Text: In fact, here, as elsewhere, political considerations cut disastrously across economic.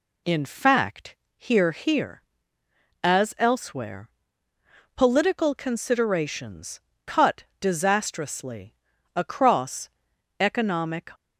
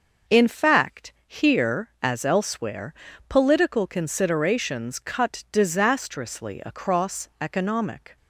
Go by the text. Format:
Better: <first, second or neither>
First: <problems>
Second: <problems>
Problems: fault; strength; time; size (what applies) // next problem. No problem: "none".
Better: second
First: says "here" twice; at 1.7 s // pauses between "considerations" and "cut"; slight; at 6.7 s; 0.27 s long // pauses between "cut" and "disastrously"; slight; at 7.4 s; 0.16 s long // pauses between "disastrously" and "across"; at 8.7 s; 0.42 s long // pauses between "across" and "economic"; noticeable; at 9.8 s; 0.50 s long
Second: none